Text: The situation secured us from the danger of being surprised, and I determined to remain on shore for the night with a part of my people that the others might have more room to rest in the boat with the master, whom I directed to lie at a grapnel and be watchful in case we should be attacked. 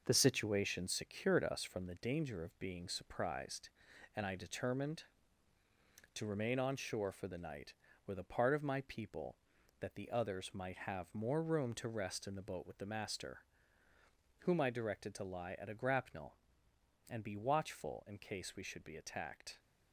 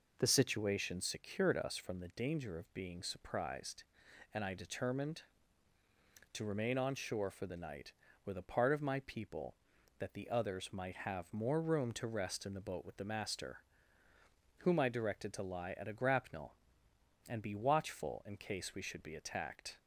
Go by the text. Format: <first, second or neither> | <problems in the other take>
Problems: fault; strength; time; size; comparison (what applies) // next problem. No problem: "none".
second | gets quieter; noticeable; throughout; 5.5 dB